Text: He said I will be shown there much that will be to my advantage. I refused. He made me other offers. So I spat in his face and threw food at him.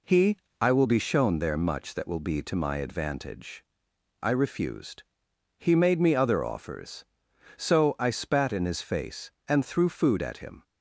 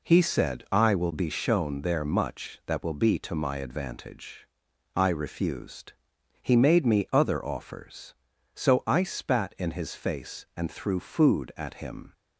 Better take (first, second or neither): second